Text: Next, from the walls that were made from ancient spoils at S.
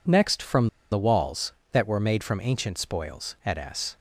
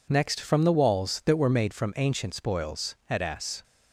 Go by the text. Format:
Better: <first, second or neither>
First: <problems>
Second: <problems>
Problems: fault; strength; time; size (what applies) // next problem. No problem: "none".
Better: second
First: pauses between "from" and "the"; slight; at 0.6 s; 0.23 s long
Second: none